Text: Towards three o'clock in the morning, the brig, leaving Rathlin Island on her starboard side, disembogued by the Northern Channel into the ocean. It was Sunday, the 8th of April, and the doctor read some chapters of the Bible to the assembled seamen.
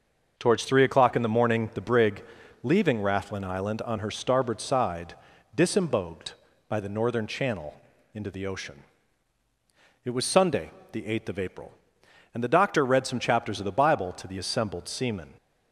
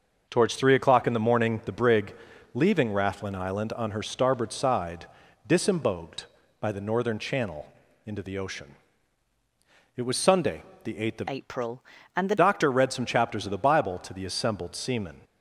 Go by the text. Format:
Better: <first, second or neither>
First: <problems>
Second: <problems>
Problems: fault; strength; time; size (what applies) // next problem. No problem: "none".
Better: first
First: starts louder than the rest; noticeable; until 1.3 s; 6 dB // pauses between "Channel" and "into"; at 7.7 s; 0.40 s long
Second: starts louder than the rest; noticeable; until 1.3 s; 6 dB // pauses between "Channel" and "into"; at 7.6 s; 0.40 s long // changes voice from "April" to "the"; from 11.2 to 12.3 s; 1.1 s long